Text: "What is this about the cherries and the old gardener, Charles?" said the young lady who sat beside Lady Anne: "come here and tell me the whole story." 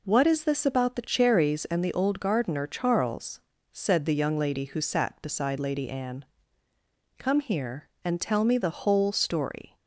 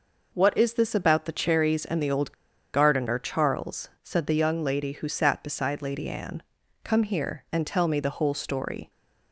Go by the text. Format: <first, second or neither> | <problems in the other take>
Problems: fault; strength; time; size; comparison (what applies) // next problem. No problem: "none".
first | pauses between "old" and "gardener"; at 2.3 s; 0.40 s long